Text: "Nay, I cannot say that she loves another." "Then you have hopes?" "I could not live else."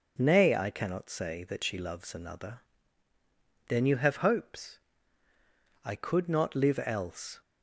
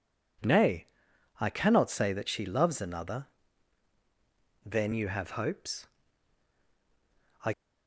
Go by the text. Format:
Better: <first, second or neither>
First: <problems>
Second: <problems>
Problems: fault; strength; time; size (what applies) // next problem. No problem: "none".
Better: first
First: none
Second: stops before "could not live else"; at 7.5 s